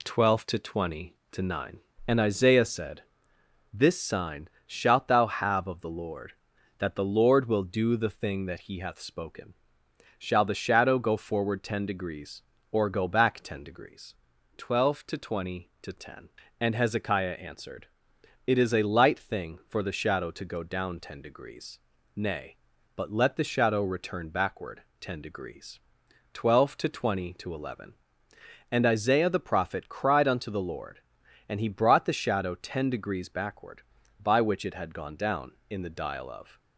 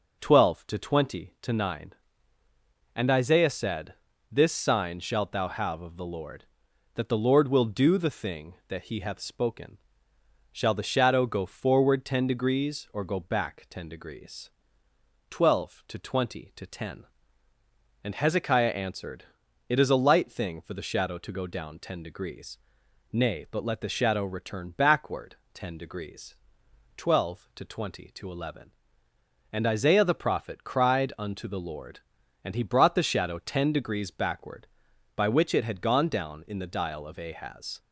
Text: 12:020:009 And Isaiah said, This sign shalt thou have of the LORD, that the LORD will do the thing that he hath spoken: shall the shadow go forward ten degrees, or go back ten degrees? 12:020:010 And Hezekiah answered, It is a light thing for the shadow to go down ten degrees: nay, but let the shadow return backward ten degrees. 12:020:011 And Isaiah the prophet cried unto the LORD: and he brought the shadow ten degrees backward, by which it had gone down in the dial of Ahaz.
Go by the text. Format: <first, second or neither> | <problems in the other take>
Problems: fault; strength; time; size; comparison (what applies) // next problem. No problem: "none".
second | pauses between "sign" and "shalt"; slight; at 4.4 s; 0.16 s long // pauses between "backward" and "ten"; slight; at 24.8 s; 0.18 s long; slight in the second // stops before "Ahaz"; at 36.5 s